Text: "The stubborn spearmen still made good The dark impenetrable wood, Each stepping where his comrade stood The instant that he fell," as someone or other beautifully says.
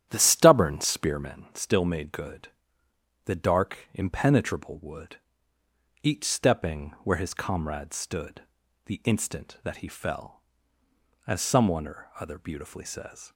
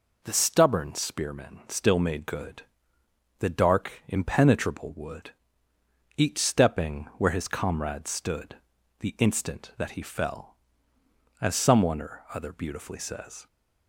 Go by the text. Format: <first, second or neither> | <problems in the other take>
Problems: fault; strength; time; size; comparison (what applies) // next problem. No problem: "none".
second | starts louder than the rest; strong; until 1.5 s; 10.5 dB // pauses between "good" and "The"; noticeable; at 2.5 s; 0.74 s long; noticeable in the second // pauses between "stood" and "The"; at 8.4 s; 0.42 s long; also in the second